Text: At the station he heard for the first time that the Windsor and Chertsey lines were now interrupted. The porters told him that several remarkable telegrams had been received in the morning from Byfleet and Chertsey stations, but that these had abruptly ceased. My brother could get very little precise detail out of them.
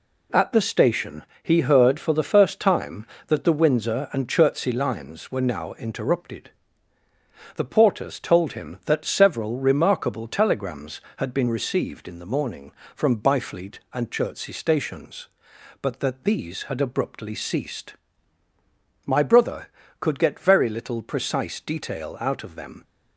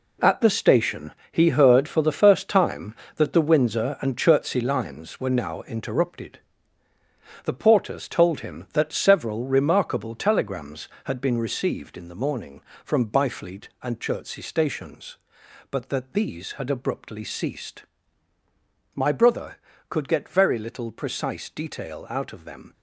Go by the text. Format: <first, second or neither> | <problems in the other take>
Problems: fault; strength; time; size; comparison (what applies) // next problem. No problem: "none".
first | gets quieter; strong; throughout; 9 dB // pauses between "station" and "he"; slight; at 1.1 s; 0.20 s long; slight in the first